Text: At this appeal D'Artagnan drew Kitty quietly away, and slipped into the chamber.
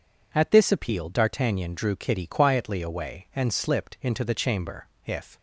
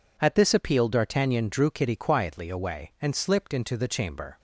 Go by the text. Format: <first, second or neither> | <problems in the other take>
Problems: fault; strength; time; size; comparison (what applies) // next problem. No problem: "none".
second | goes on to say "If"; slight; from 5.0 s on; 0.32 s long